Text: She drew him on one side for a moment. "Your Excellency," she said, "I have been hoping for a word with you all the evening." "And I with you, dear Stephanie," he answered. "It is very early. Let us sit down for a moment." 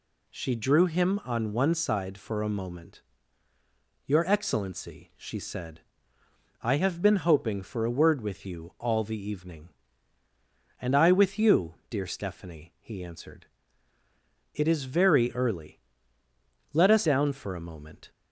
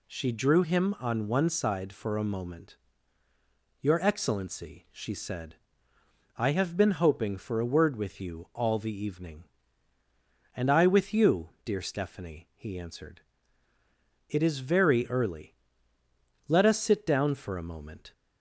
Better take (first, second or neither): second